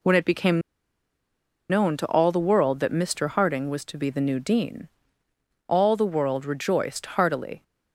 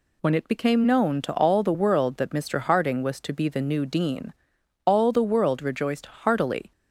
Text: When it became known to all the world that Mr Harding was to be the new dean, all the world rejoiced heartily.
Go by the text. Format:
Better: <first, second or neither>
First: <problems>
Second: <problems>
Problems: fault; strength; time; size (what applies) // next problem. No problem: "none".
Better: second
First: pauses between "became" and "known"; at 0.6 s; 1.0 s long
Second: none